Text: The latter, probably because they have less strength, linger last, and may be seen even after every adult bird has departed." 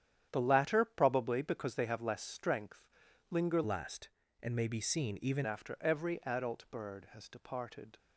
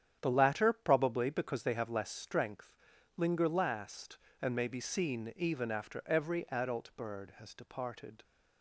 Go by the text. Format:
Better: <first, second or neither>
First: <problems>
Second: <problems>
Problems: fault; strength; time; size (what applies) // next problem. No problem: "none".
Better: second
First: starts louder than the rest; strong; until 1.3 s; 9.5 dB // changes voice from "last" to "even"; from 3.6 to 5.4 s; 1.8 s long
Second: starts louder than the rest; strong; until 1.2 s; 9.5 dB